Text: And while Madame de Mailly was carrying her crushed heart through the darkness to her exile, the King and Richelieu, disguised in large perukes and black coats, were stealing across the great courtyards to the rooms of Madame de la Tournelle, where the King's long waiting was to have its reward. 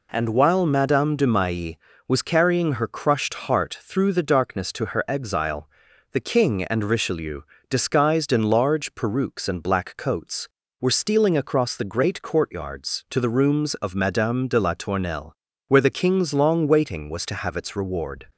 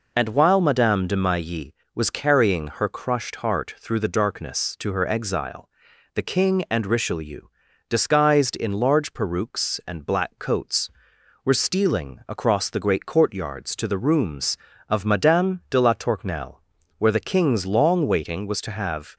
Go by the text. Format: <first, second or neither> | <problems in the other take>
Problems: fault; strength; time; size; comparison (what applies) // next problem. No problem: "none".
first | stops before "its reward"; at 19.1 s